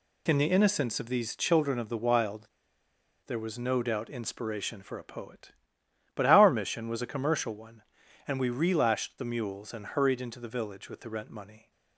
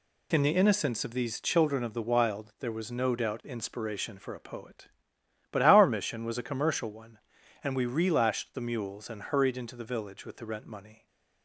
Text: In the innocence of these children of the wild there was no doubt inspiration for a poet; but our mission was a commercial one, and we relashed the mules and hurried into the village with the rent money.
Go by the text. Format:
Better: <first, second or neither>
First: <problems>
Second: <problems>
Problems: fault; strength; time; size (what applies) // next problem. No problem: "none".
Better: second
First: pauses between "wild" and "there"; noticeable; at 2.4 s; 0.79 s long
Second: none